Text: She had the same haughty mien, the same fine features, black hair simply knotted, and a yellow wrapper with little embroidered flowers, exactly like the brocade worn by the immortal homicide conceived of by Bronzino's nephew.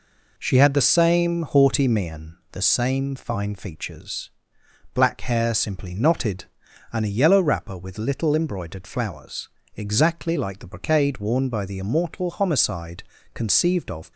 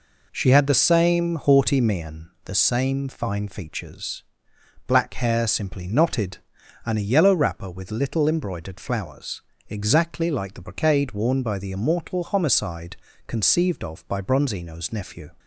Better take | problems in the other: second | pauses between "homicide" and "conceived"; slight; at 13.0 s; 0.30 s long; slight in the second // stops before "by Bronzino's nephew"; at 14.1 s

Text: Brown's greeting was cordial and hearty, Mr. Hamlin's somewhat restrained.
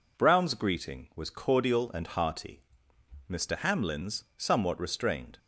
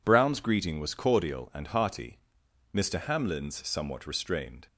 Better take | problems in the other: neither | none

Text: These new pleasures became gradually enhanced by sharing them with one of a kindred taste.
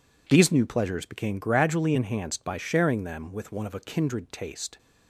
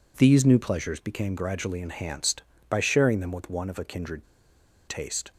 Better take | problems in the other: first | pauses between "kindred" and "taste"; noticeable; at 4.2 s; 0.63 s long

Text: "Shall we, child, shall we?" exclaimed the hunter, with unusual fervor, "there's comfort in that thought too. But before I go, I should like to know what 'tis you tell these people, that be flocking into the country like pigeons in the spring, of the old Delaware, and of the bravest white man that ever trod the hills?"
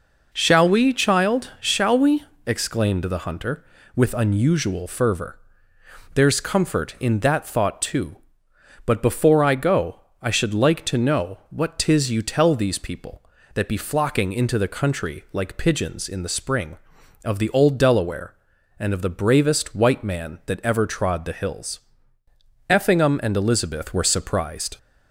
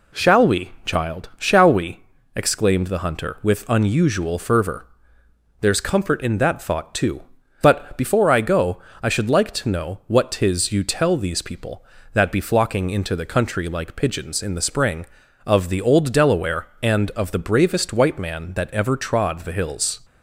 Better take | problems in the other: second | goes on to say "Effingham and Elizabeth were surprised"; strong; from 22.6 s on; 2.0 s long

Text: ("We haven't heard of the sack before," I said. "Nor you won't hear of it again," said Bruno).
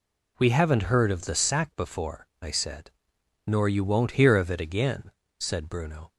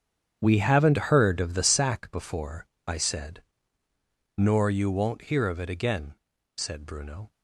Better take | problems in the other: first | gets quieter; strong; throughout; 14 dB

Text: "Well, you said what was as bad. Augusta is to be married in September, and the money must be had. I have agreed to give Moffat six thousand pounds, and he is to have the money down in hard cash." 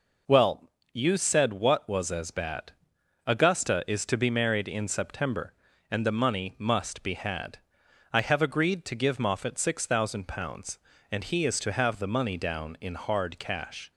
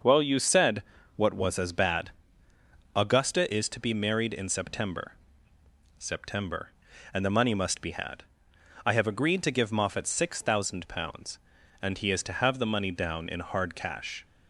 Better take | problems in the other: first | starts louder than the rest; until 1.3 s; 6 dB // pauses between "said" and "what"; slight; at 0.8 s; 0.34 s long // says "September" twice; at 5.9 s

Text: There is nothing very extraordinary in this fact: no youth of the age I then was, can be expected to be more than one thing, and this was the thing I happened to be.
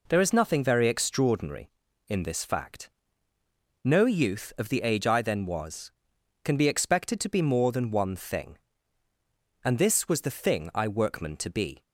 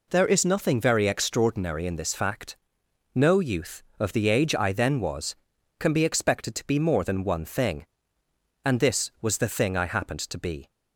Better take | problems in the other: second | says "workman" for "happened"; at 10.8 s

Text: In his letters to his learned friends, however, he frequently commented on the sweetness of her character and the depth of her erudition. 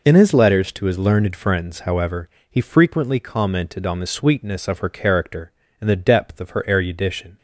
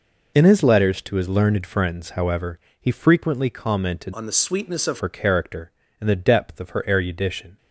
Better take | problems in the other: first | changes voice from "on" to "of"; from 4.1 to 4.9 s; 0.8 s long

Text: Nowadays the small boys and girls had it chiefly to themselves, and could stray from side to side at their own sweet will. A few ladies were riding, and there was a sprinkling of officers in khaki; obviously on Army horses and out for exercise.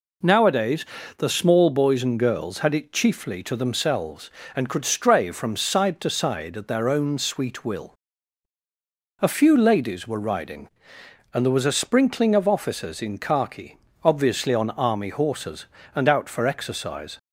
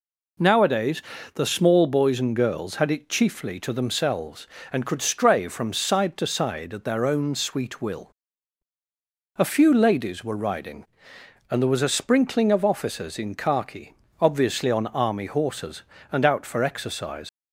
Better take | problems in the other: first | pauses between "Nowadays" and "the"; slight; at 1.0 s; 0.32 s long; slight in the first // leaves "exercise" unfinished; at 17.2 s; 50 ms

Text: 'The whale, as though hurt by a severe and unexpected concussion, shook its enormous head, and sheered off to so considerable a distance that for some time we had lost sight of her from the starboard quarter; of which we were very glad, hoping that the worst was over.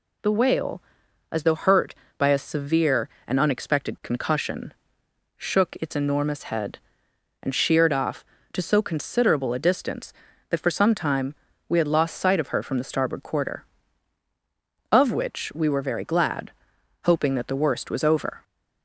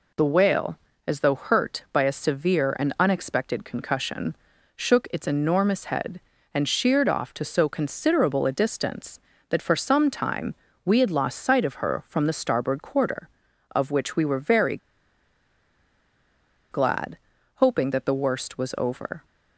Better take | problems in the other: first | pauses between "time" and "we"; slight; at 10.5 s; 0.30 s long; slight in the first // pauses between "very" and "glad"; strong; at 14.7 s; 1.9 s long

